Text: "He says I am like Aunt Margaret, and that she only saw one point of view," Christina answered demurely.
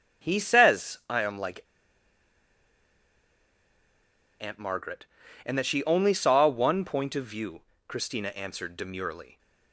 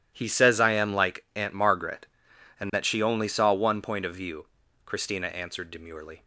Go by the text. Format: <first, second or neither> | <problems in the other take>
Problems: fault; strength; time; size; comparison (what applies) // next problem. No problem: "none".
second | starts louder than the rest; strong; until 1.3 s; 10.5 dB // pauses between "like" and "Aunt"; strong; at 1.6 s; 2.7 s long